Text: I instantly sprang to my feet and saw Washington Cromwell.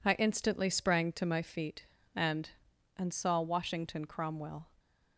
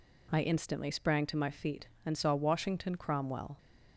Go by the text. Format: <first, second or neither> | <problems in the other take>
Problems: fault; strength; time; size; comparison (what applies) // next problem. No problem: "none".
second | says "and" twice; at 2.9 s